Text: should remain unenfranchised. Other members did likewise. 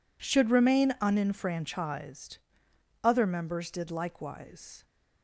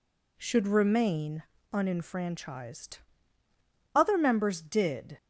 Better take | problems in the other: first | pauses between "remain" and "unenfranchised"; slight; at 1.4 s; 0.30 s long // stops before "likewise"; at 5.1 s

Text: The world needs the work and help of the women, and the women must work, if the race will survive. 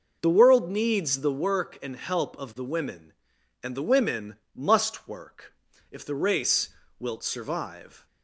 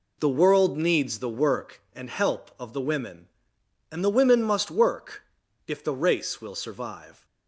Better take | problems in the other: second | pauses between "women" and "must"; slight; at 4.3 s; 0.18 s long // says "wilt" for "will"; at 6.9 s

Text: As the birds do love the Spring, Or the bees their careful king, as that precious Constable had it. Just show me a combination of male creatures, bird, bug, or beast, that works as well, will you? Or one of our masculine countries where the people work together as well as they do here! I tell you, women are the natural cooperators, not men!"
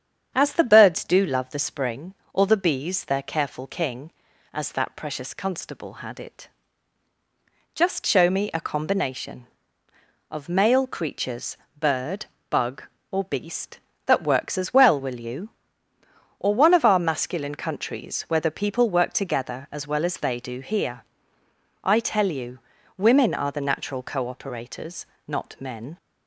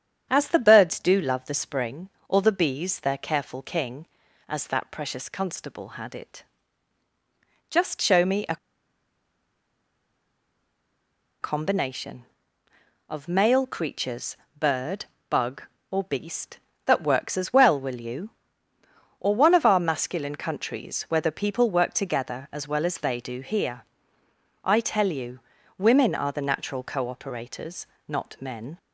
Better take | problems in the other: first | starts louder than the rest; strong; until 1.3 s; 8 dB; strong in the first // pauses between "a" and "combination"; strong; at 8.5 s; 2.8 s long

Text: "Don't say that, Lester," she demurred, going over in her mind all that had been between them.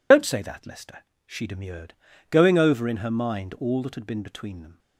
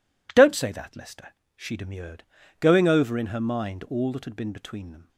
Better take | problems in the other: second | loses the start of "Don't"; at 0.1 s; 110 ms

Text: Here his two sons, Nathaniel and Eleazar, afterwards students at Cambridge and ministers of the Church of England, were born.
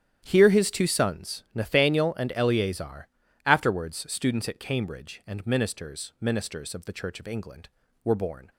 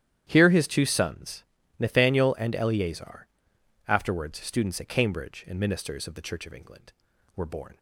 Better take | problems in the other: second | starts louder than the rest; strong; until 1.2 s; 10 dB; strong in the second // says "ministers" twice; at 6.1 s

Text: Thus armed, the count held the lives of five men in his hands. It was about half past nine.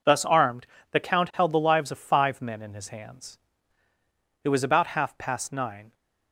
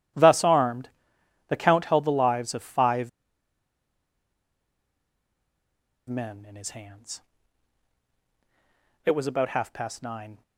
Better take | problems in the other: first | pauses between "five" and "men"; strong; at 3.0 s; 2.9 s long

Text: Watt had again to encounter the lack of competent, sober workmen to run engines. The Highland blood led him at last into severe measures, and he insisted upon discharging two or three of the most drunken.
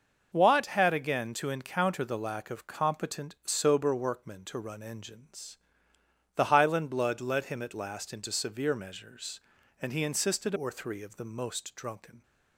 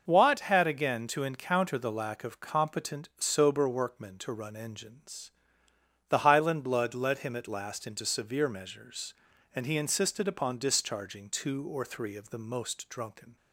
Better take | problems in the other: second | starts louder than the rest; noticeable; until 1.3 s; 6 dB; noticeable in the second // skips "upon discharging two"; at 10.5 s

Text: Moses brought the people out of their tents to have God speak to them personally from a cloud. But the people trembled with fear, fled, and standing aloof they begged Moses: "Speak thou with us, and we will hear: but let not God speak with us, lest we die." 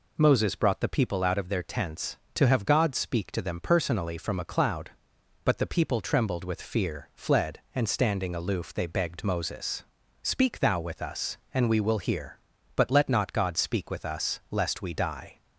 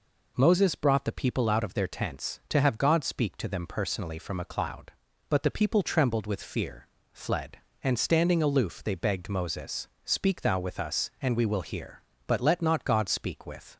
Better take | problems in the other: first | stops before "us lest we die"; at 13.7 s

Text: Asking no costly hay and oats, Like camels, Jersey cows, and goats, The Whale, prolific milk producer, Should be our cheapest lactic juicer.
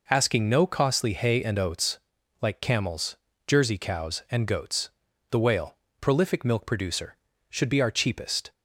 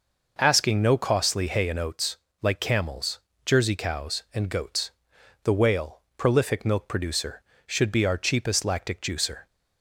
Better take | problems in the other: second | stops before "lactic juicer"; at 8.5 s

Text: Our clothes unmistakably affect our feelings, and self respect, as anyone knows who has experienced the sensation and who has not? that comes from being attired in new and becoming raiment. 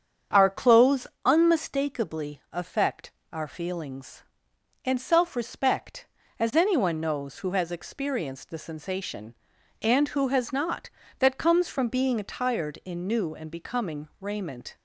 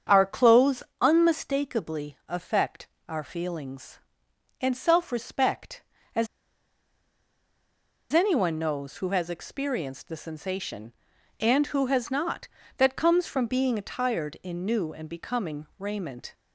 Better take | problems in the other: first | starts louder than the rest; strong; until 1.3 s; 8 dB; strong in the first // pauses between "clothes" and "unmistakably"; slight; at 0.8 s; 0.20 s long; slight in the first // pauses between "affect" and "our"; slight; at 2.8 s; 0.22 s long; slight in the first // pauses between "as" and "anyone"; strong; at 6.2 s; 1.8 s long

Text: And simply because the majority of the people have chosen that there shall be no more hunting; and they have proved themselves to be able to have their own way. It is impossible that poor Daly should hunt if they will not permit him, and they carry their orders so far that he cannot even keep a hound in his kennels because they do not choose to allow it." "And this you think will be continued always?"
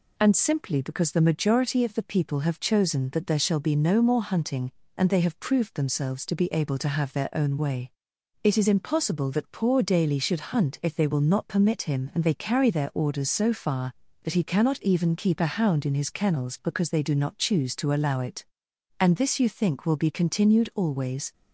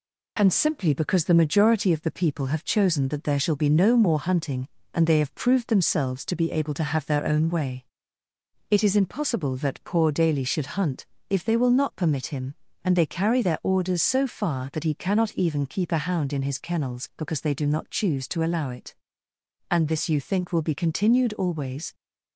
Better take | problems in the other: first | gets quieter; slight; throughout; 2.5 dB // pauses between "hunt" and "if"; slight; at 11.0 s; 0.20 s long

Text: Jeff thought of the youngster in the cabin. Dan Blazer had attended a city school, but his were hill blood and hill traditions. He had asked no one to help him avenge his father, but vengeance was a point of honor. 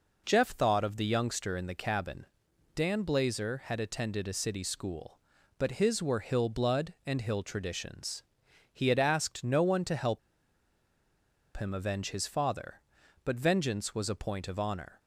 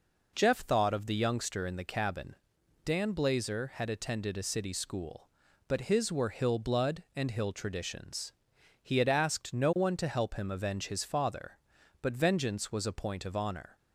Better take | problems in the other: second | pauses between "help" and "him"; strong; at 10.1 s; 1.3 s long

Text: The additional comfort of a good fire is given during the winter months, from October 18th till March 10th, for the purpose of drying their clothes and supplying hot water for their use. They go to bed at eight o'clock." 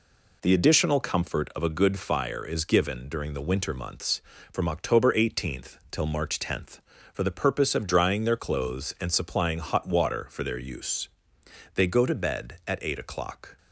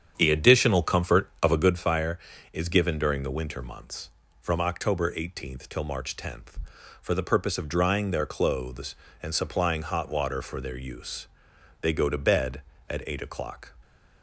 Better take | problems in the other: first | starts louder than the rest; strong; until 1.8 s; 8 dB

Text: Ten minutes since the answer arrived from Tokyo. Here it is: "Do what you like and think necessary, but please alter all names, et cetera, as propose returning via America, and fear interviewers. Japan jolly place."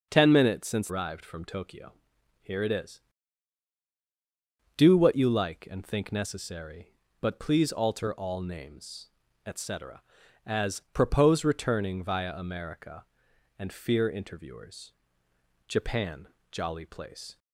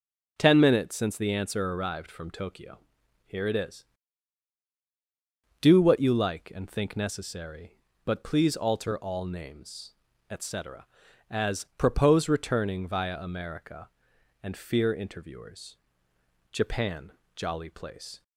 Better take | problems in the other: second | starts louder than the rest; until 1.1 s; 6.5 dB // skips "the answer"; at 0.8 s // pauses between "Japan" and "jolly"; slight; at 16.2 s; 0.22 s long; slight in the second

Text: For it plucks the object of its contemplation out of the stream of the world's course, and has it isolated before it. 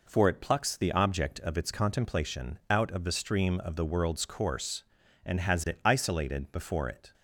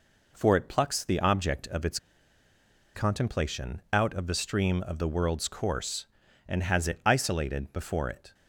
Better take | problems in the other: first | pauses between "its" and "contemplation"; at 1.9 s; 0.98 s long

